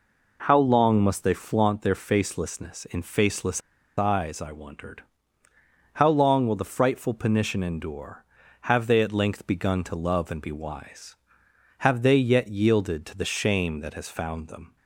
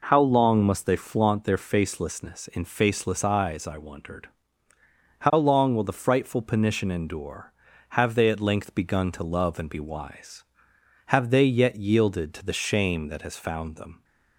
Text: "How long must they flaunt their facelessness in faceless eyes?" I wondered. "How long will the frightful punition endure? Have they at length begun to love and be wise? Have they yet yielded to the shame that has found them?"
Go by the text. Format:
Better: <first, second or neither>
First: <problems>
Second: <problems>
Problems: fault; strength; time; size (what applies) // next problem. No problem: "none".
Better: second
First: pauses between "faceless" and "eyes"; at 3.6 s; 0.36 s long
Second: none